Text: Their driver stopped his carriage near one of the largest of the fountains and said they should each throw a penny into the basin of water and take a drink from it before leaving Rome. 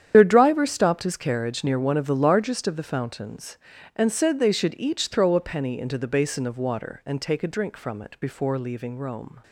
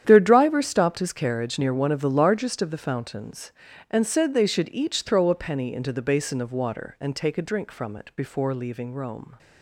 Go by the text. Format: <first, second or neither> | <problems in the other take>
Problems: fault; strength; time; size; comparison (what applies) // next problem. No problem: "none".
second | loses the start of "Their"; at 0.1 s; 50 ms // starts louder than the rest; strong; until 1.1 s; 9 dB; strong in the second